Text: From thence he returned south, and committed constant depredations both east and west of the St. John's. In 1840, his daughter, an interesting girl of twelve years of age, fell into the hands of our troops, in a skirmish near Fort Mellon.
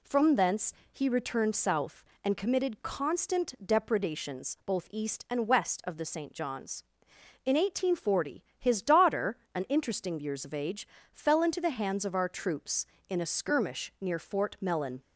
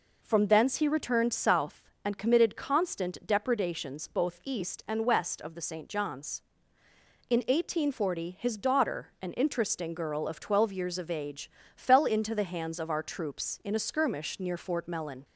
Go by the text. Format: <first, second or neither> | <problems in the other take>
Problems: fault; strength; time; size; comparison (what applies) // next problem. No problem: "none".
second | pauses between "thence" and "he"; slight; at 0.7 s; 0.18 s long // skips "girl of twelve"; at 10.1 s